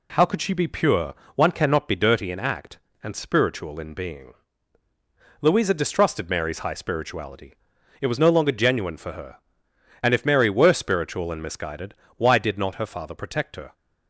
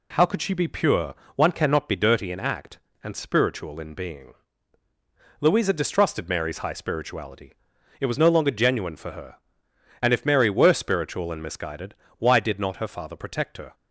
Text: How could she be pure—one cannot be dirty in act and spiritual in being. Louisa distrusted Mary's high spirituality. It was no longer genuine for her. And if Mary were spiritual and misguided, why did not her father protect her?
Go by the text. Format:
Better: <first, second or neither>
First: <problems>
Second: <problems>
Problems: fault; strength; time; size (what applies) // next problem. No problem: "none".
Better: neither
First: none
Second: none